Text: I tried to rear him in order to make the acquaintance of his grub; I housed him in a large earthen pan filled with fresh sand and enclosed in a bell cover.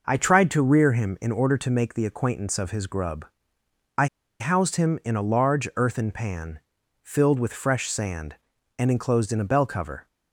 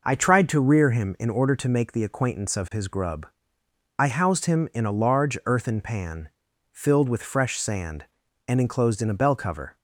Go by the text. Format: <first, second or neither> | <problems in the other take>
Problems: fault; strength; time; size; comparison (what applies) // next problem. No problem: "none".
second | pauses between "I" and "housed"; slight; at 4.0 s; 0.34 s long // pauses between "pan" and "filled"; at 6.5 s; 0.42 s long; also in the second